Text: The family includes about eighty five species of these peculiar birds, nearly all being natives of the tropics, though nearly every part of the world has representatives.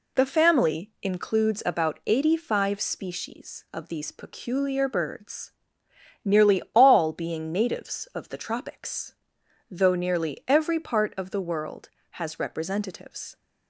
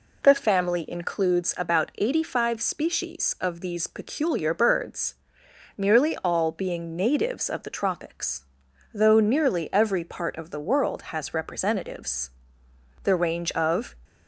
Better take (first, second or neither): first